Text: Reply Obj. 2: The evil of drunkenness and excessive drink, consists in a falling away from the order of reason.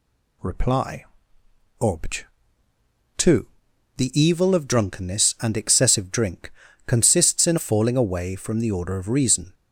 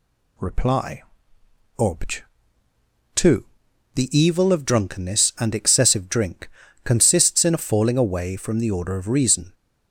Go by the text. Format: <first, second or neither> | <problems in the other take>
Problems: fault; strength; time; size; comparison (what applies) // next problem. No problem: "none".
second | pauses between "Reply" and "Obj"; noticeable; at 1.0 s; 0.78 s long; noticeable in the second // skips "a"; at 7.5 s